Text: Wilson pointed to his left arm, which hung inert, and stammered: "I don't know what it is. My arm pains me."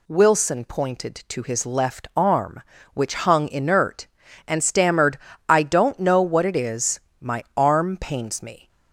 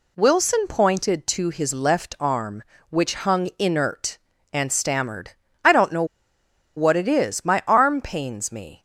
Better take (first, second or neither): first